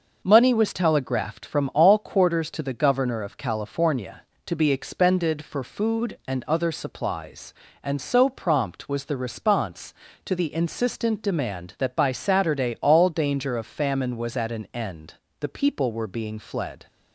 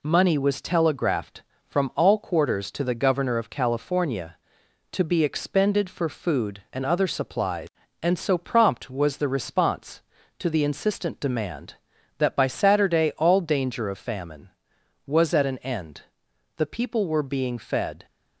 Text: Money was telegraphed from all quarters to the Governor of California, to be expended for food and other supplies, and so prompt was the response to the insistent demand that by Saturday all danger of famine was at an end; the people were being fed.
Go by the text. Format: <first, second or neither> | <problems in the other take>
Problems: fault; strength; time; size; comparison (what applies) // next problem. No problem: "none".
second | says "fled" for "fed"; at 16.3 s